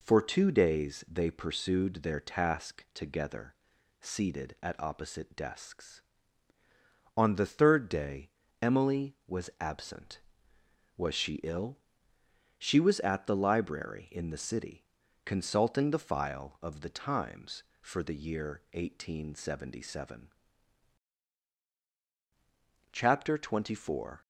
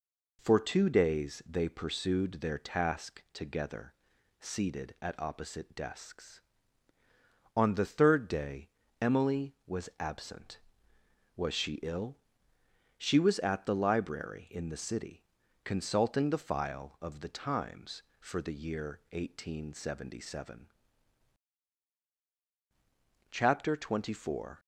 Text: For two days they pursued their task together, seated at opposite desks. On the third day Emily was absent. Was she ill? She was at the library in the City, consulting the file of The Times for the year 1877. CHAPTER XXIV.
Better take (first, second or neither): neither